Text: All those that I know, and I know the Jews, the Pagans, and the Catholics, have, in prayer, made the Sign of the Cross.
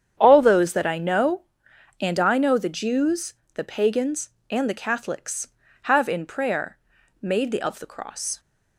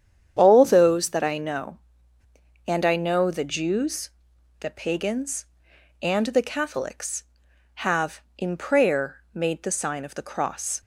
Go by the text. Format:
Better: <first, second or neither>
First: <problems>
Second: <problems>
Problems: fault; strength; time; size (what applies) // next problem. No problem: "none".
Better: second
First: starts louder than the rest; strong; until 1.1 s; 8.5 dB // skips "Sign"; at 7.6 s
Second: starts louder than the rest; strong; until 1.3 s; 8.5 dB